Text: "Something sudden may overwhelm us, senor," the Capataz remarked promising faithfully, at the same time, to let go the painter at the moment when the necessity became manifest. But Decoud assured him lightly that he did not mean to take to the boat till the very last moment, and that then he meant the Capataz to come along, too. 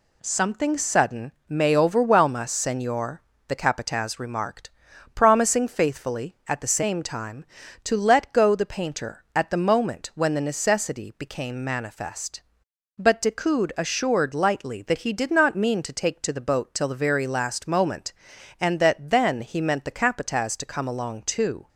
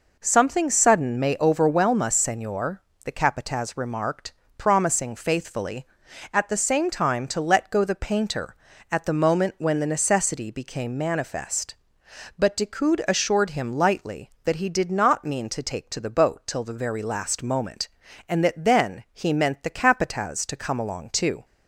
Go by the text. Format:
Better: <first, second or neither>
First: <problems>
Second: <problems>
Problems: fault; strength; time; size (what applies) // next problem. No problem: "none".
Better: second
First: pauses between "sudden" and "may"; slight; at 1.3 s; 0.16 s long // pauses between "remarked" and "promising"; at 4.6 s; 0.44 s long // skips "him"; at 14.3 s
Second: pauses between "remarked" and "promising"; slight; at 4.3 s; 0.26 s long